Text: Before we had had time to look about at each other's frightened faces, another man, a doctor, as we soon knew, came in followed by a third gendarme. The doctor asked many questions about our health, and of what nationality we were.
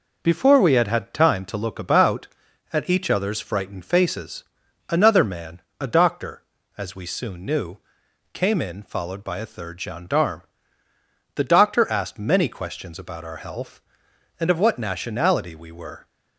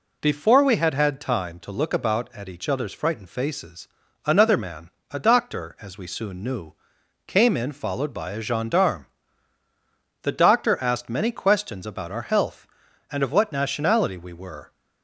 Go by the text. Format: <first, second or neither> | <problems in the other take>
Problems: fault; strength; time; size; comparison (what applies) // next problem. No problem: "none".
first | skips "third"; at 8.4 s